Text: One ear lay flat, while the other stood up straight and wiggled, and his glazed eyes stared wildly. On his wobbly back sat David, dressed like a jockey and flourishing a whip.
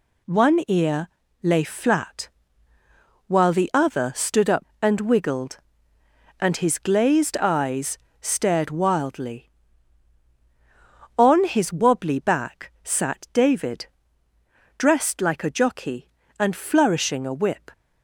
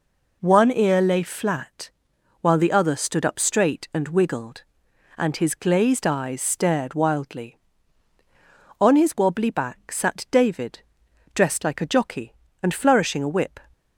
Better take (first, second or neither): second